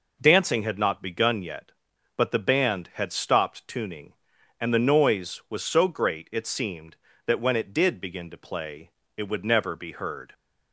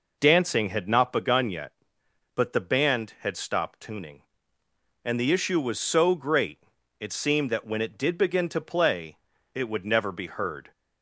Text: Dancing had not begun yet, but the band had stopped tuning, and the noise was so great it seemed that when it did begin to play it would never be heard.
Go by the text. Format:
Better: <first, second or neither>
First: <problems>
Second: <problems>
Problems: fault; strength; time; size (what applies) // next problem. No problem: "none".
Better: first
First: pauses between "play" and "it"; slight; at 8.8 s; 0.26 s long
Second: says "issue" for "noise"; at 5.3 s // pauses between "great" and "it"; at 6.5 s; 0.40 s long // pauses between "play" and "it"; at 9.1 s; 0.38 s long